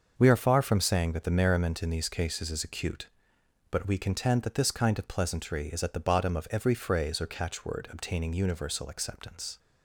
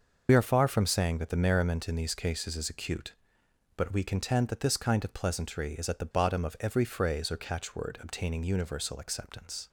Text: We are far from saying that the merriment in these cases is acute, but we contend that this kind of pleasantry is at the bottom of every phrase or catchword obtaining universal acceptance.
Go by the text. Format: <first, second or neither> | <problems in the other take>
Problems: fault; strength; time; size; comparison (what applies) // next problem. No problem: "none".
first | loses the start of "We"; at 0.2 s; 55 ms // starts louder than the rest; noticeable; until 1.3 s; 6 dB; also in the first